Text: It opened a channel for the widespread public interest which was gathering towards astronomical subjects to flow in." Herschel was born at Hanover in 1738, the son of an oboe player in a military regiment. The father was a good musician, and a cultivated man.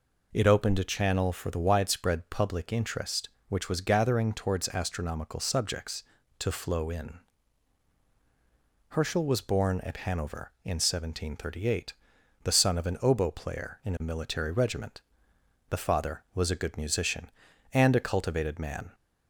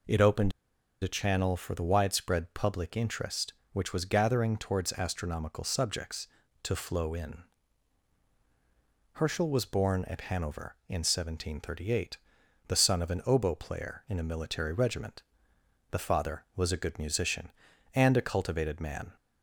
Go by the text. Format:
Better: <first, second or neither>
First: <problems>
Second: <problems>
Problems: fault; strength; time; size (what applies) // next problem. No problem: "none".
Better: first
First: none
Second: pauses between "opened" and "a"; noticeable; at 0.5 s; 0.51 s long